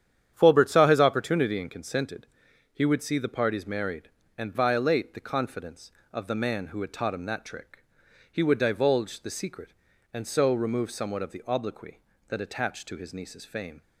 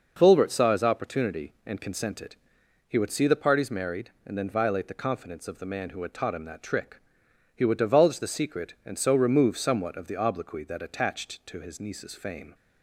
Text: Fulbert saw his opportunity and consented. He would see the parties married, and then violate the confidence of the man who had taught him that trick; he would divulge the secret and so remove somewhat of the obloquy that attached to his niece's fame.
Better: second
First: starts louder than the rest; strong; until 1.3 s; 9.5 dB // skips "then"; at 4.5 s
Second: none

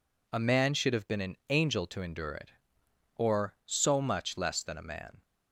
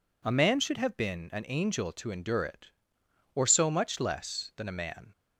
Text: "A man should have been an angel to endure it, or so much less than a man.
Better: neither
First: none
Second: none

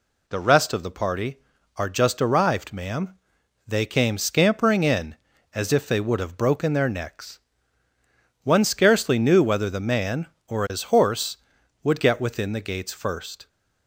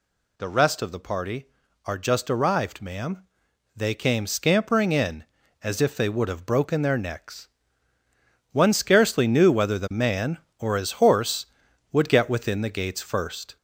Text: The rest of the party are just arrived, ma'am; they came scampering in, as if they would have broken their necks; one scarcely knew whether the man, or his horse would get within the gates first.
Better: first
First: none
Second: gets louder; throughout; 3.5 dB

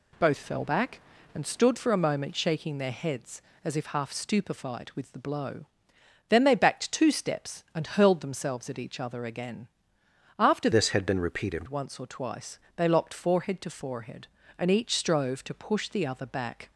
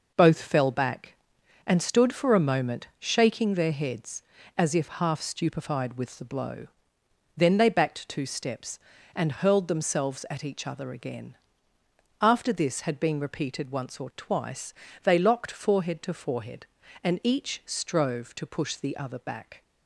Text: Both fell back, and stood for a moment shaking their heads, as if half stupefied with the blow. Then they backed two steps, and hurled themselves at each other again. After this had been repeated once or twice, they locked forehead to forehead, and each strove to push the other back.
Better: second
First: changes voice from "this" to "repeated"; from 10.7 to 11.6 s; 0.9 s long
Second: none

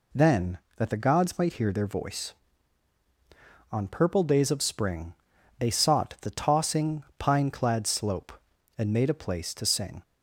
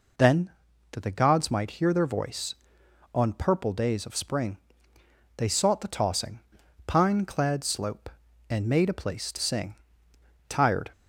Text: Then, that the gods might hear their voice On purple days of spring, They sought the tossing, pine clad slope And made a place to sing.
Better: first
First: none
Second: goes on to say "Tired"; slight; from 10.4 s on; 0.44 s long

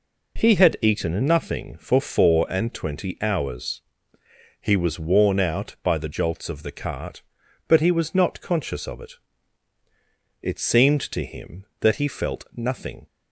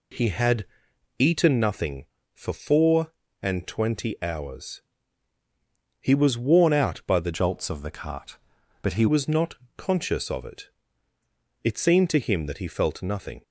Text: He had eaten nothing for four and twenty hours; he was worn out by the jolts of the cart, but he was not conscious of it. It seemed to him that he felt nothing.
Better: first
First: none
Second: pauses between "had" and "eaten"; noticeable; at 0.6 s; 0.52 s long // changes voice from "jolts" to "he"; from 7.3 to 9.0 s; 1.7 s long // pauses between "not" and "conscious"; slight; at 9.5 s; 0.20 s long

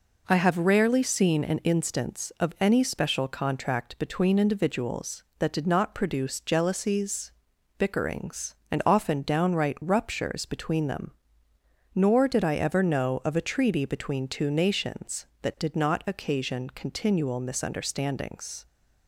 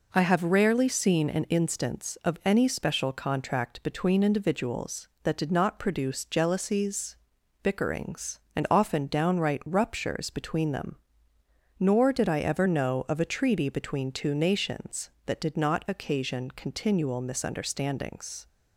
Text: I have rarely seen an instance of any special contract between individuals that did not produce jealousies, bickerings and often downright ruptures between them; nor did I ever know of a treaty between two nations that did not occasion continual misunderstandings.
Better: neither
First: none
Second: none

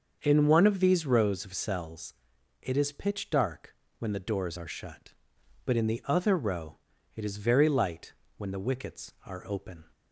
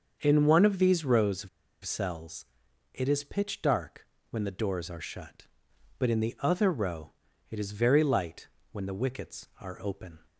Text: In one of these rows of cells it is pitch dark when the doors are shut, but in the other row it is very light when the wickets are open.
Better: first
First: starts louder than the rest; until 1.2 s; 6.5 dB // pauses between "cells" and "it"; noticeable; at 2.1 s; 0.48 s long // pauses between "dark" and "when"; slight; at 3.7 s; 0.26 s long // pauses between "row" and "it"; slight; at 6.7 s; 0.36 s long // pauses between "light" and "when"; slight; at 8.1 s; 0.24 s long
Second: starts louder than the rest; until 1.2 s; 6.5 dB // pauses between "of" and "cells"; slight; at 1.4 s; 0.35 s long // pauses between "cells" and "it"; noticeable; at 2.4 s; 0.48 s long // pauses between "dark" and "when"; slight; at 4.0 s; 0.26 s long // pauses between "row" and "it"; slight; at 7.1 s; 0.36 s long // pauses between "light" and "when"; slight; at 8.4 s; 0.24 s long

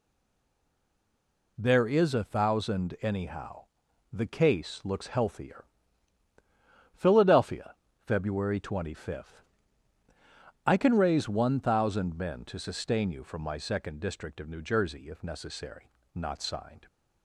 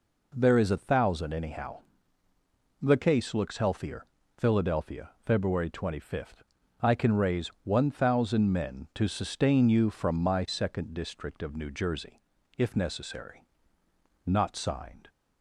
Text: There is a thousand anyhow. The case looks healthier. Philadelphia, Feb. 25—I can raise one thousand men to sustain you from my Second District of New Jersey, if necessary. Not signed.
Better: second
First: stays silent before the first word; noticeable; until 1.5 s; 1.5 s long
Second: none

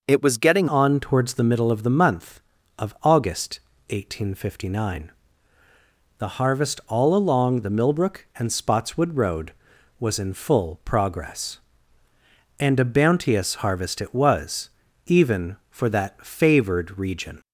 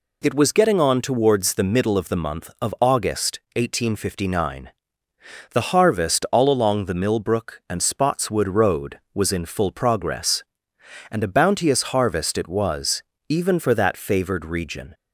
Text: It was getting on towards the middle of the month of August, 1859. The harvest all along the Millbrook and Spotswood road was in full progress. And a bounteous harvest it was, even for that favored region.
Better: second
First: changes voice at "on"; from 0.6 s on; 16.8 s long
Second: none

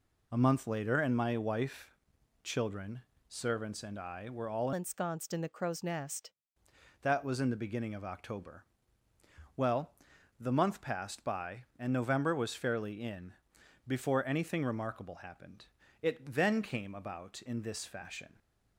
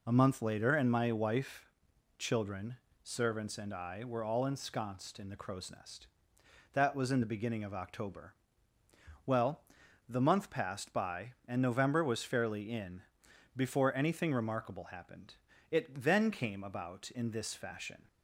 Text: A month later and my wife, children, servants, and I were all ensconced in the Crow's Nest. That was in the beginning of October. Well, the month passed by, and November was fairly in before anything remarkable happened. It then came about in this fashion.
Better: second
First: changes voice from "ensconced" to "Nest"; from 4.7 to 6.3 s; 1.6 s long // pauses between "in" and "before"; noticeable; at 13.3 s; 0.54 s long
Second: pauses between "in" and "before"; noticeable; at 13.0 s; 0.54 s long

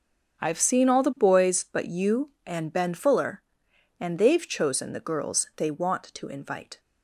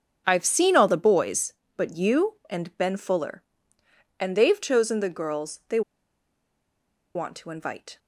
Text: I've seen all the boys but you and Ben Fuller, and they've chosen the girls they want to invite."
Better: first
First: starts louder than the rest; until 1.4 s; 6.5 dB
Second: starts louder than the rest; strong; until 1.2 s; 7.5 dB // pauses between "they" and "want"; strong; at 5.8 s; 1.3 s long

